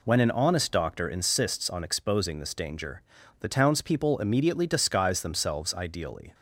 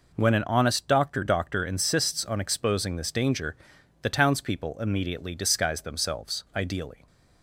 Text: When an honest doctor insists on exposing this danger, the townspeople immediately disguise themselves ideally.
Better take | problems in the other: first | says "doctor" twice; at 1.2 s

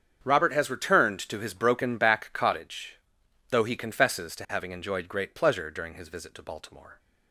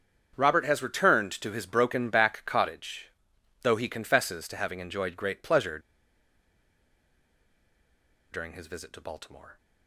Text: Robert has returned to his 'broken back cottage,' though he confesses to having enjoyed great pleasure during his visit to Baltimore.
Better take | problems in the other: first | starts louder than the rest; strong; until 1.3 s; 7.5 dB; strong in the first // pauses between "pleasure" and "during"; strong; at 5.7 s; 2.5 s long

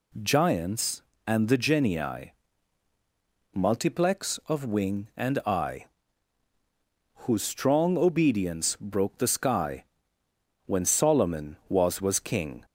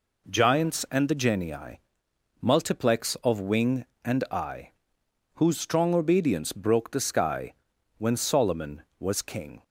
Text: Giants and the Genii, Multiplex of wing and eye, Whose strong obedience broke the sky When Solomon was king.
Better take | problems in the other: second | pauses between "sky" and "When"; noticeable; at 9.8 s; 0.82 s long; also in the second // says "was" twice; at 12.0 s

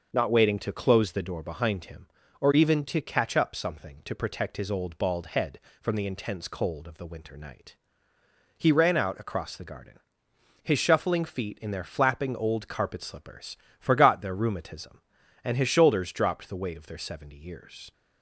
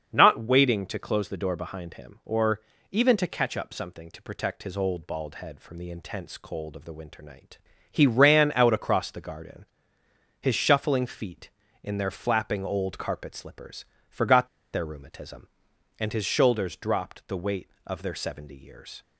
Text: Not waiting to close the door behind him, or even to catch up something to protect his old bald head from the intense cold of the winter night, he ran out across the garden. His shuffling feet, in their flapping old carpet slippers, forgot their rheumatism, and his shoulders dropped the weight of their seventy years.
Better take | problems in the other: first | starts louder than the rest; until 1.1 s; 7 dB // pauses between "or" and "even"; slight; at 2.6 s; 0.30 s long // pauses between "forgot" and "their"; slight; at 14.4 s; 0.25 s long

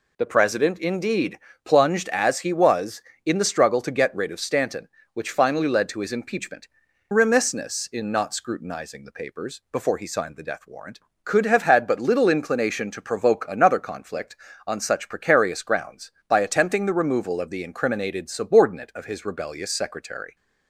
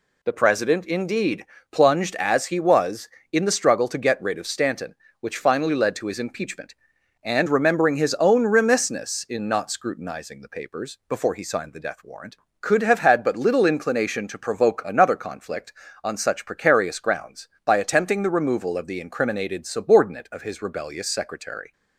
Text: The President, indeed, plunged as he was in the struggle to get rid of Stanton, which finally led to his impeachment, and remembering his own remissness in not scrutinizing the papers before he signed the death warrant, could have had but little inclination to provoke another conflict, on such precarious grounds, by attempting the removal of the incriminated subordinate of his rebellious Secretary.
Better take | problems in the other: second | skips "and remembering his own"; at 6.8 s

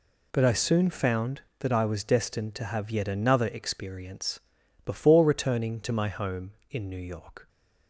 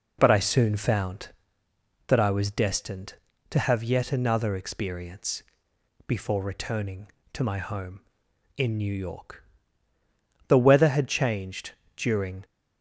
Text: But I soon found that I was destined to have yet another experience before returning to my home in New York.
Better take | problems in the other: first | pauses between "experience" and "before"; noticeable; at 5.4 s; 0.64 s long; also in the first // goes on to say "The weather had changed during"; strong; from 10.4 s on; 1.9 s long

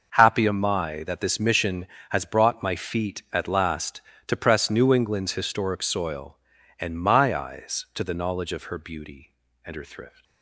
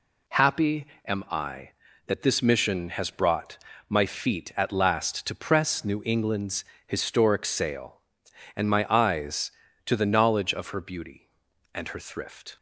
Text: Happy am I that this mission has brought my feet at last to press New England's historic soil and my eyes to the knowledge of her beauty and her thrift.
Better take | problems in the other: first | pauses between "Happy" and "am"; slight; at 0.8 s; 0.18 s long // pauses between "brought" and "my"; slight; at 3.5 s; 0.32 s long // pauses between "England's" and "historic"; slight; at 6.6 s; 0.22 s long // says "sail" for "soil"; at 7.4 s

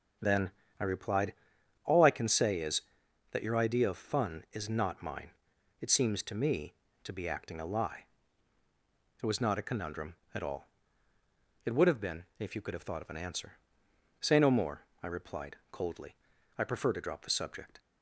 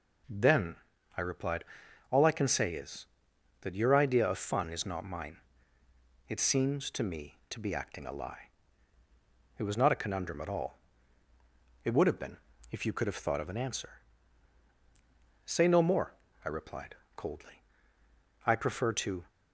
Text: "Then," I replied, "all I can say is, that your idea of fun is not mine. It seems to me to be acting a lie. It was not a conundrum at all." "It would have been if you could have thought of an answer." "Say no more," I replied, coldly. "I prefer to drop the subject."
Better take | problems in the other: first | pauses between "been" and "if"; slight; at 12.3 s; 0.34 s long // stops before "drop the subject"; at 19.2 s

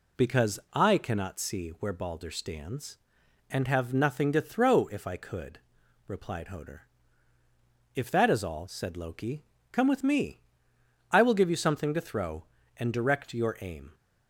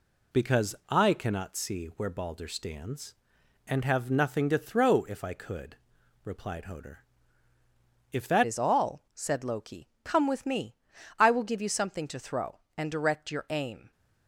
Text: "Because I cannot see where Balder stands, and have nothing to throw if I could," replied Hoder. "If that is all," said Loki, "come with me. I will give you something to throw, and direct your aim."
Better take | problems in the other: first | changes voice at "is"; from 8.4 s on; 5.5 s long

